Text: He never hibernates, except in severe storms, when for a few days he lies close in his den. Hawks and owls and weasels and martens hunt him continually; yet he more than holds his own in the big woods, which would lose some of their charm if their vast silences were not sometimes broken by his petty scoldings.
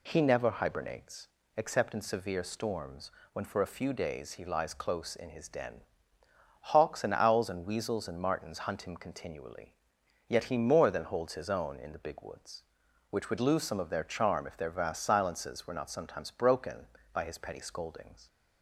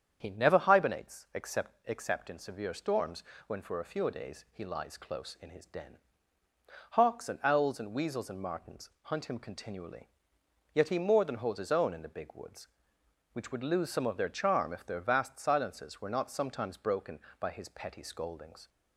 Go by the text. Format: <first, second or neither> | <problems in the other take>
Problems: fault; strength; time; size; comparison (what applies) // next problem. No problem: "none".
first | starts louder than the rest; strong; until 1.2 s; 8 dB // says "except" twice; at 1.8 s